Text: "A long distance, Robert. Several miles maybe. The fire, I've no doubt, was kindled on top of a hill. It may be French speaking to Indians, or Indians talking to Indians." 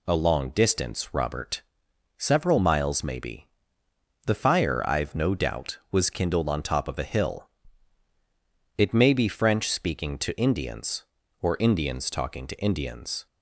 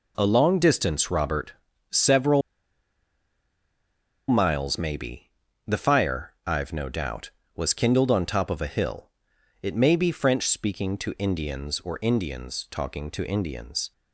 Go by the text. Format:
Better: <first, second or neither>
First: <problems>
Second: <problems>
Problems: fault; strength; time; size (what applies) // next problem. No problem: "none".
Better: first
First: none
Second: pauses between "Several" and "miles"; strong; at 2.4 s; 1.8 s long